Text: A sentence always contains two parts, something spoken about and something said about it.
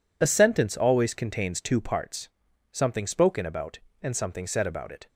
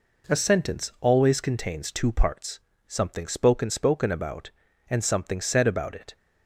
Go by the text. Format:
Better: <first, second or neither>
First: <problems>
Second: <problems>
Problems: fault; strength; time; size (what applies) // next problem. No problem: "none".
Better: first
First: none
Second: says "spoken" twice; at 3.6 s